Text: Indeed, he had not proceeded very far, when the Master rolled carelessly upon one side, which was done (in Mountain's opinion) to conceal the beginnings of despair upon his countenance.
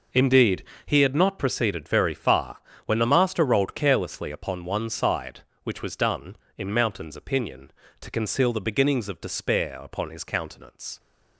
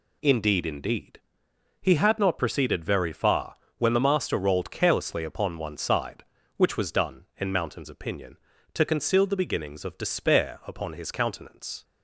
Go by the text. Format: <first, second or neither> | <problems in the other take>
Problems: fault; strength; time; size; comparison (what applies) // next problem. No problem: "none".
first | says "Indeed" twice; at 0.6 s